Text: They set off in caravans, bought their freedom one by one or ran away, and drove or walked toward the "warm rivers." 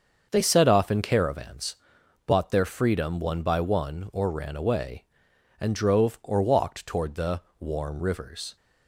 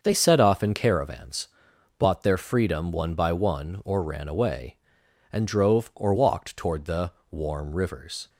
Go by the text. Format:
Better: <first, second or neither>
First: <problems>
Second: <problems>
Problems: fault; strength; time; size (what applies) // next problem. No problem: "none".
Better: neither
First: starts louder than the rest; until 1.3 s; 6.5 dB // pauses between "the" and "warm"; slight; at 7.4 s; 0.19 s long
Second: starts louder than the rest; until 1.0 s; 6.5 dB // pauses between "the" and "warm"; slight; at 7.1 s; 0.20 s long